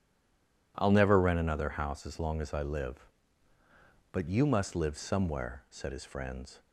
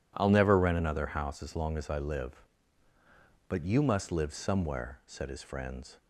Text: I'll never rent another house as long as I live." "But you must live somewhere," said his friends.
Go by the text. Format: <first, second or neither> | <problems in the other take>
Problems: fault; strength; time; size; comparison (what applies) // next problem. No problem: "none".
second | stays silent before the first word; slight; until 0.7 s; 0.7 s long